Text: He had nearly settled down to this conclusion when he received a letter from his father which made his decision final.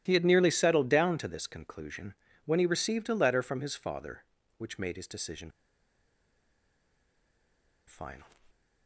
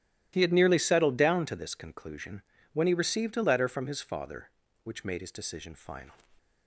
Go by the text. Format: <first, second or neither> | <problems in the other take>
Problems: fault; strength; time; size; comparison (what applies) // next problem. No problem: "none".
second | starts louder than the rest; strong; until 1.0 s; 13 dB; strong in the second // pauses between "conclusion" and "when"; slight; at 2.1 s; 0.30 s long; slight in the second // pauses between "decision" and "final"; strong; at 5.5 s; 2.3 s long